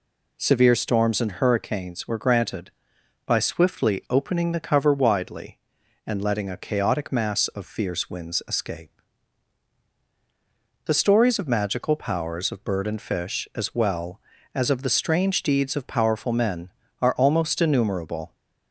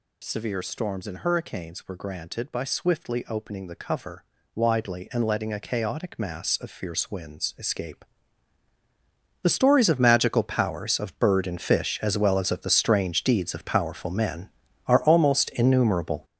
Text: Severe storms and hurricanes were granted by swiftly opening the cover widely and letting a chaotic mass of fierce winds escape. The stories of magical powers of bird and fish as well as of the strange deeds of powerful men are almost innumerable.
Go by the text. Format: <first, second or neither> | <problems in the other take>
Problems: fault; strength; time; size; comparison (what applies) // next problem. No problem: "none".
first | gets louder; strong; throughout; 9 dB // pauses between "cover" and "widely"; slight; at 4.2 s; 0.32 s long